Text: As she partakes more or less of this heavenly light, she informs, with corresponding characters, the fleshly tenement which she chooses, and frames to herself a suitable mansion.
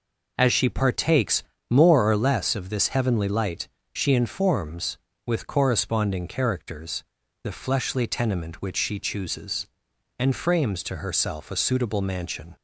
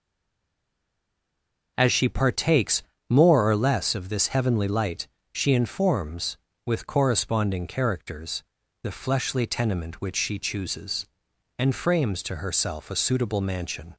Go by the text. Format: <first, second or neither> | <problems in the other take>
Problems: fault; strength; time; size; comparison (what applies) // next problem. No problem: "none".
first | stays silent before the first word; noticeable; until 1.7 s; 1.7 s long // pauses between "partakes" and "more"; slight; at 2.8 s; 0.26 s long; slight in the first